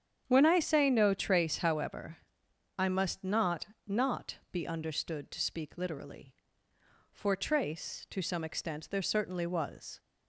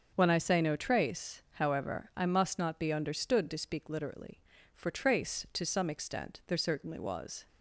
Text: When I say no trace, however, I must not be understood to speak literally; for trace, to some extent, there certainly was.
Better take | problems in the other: second | starts louder than the rest; strong; until 1.2 s; 8.5 dB; also in the second // says "not" twice; at 3.8 s

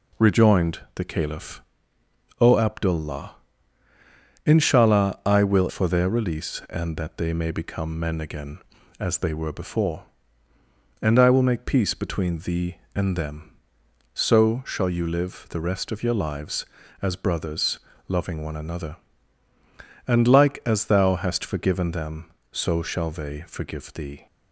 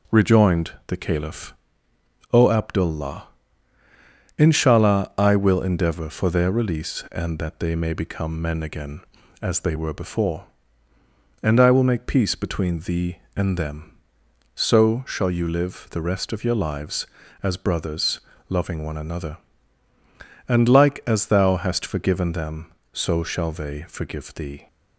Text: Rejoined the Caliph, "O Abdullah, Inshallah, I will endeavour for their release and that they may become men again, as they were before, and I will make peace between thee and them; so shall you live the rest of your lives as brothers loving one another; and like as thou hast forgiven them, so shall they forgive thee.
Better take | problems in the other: second | pauses between "Rejoined" and "the"; slight; at 0.7 s; 0.16 s long; slight in the second // skips "endeavour"; at 5.6 s // pauses between "brothers" and "loving"; slight; at 17.7 s; 0.28 s long; slight in the second

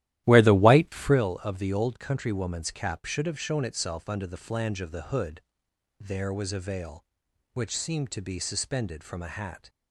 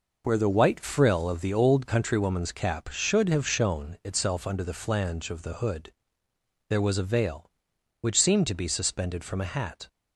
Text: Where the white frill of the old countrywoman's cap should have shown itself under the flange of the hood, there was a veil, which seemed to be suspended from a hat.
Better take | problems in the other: second | starts louder than the rest; strong; until 1.3 s; 14 dB

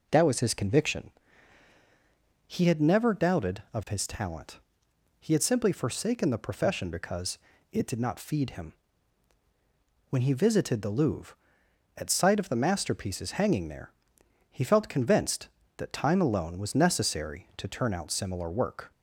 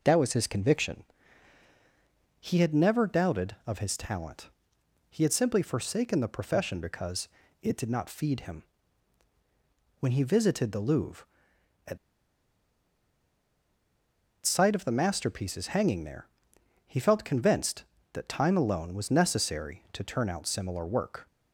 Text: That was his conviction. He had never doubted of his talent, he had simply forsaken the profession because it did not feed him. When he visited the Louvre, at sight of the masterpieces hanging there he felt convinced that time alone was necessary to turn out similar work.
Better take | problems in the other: first | pauses between "because" and "it"; slight; at 7.2 s; 0.34 s long; slight in the first // pauses between "at" and "sight"; strong; at 11.9 s; 2.4 s long // pauses between "there" and "he"; noticeable; at 16.2 s; 0.58 s long; noticeable in the first

